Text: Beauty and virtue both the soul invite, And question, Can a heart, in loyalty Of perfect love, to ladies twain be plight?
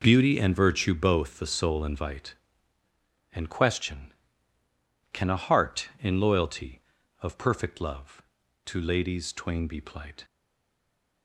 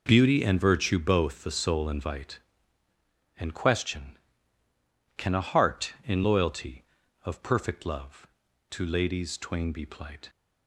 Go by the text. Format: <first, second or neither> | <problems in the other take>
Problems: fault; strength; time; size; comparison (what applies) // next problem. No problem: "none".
second | stays silent after the last word; from 10.2 s on; 1.0 s long